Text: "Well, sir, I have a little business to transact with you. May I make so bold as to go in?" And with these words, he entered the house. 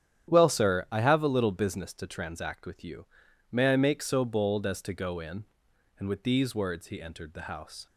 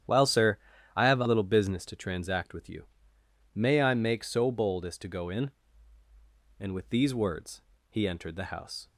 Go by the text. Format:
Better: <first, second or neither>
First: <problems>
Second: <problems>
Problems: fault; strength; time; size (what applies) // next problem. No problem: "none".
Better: neither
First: starts louder than the rest; strong; until 1.3 s; 10 dB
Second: starts louder than the rest; strong; until 1.4 s; 10 dB